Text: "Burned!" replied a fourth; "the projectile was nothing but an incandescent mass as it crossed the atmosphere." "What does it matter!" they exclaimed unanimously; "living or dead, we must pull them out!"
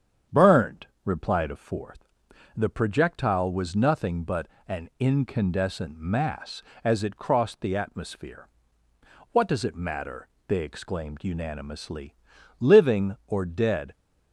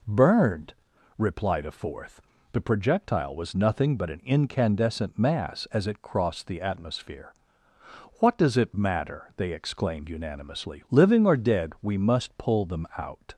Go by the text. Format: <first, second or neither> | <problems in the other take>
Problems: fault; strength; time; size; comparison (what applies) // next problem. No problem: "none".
second | starts louder than the rest; strong; until 1.4 s; 8 dB // pauses between "but" and "an"; slight; at 4.4 s; 0.22 s long // stops before "we must pull them out"; at 13.9 s